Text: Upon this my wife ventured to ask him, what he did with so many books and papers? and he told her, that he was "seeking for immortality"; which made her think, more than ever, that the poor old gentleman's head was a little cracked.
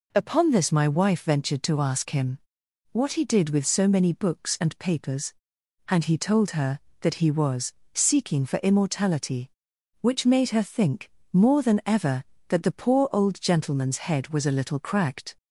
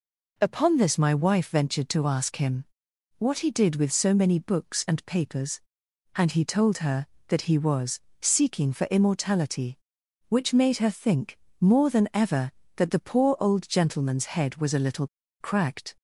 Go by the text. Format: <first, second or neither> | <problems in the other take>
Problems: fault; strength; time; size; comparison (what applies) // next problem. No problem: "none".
first | pauses between "was" and "seeking"; slight; at 8.0 s; 0.20 s long; slight in the first // pauses between "little" and "cracked"; slight; at 15.0 s; 0.34 s long